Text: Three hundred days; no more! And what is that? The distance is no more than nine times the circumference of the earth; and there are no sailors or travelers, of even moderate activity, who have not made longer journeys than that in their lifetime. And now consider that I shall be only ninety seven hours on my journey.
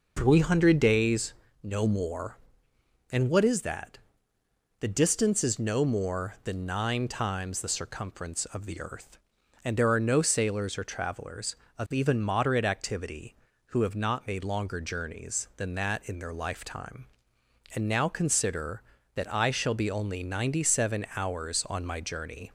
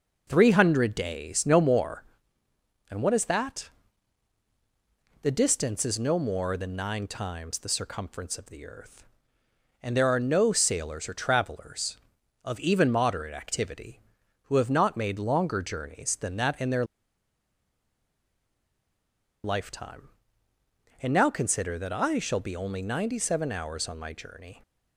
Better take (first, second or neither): first